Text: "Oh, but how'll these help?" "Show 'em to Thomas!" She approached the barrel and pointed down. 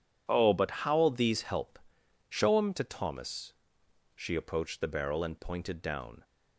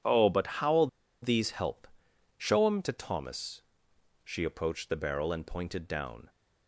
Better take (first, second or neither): first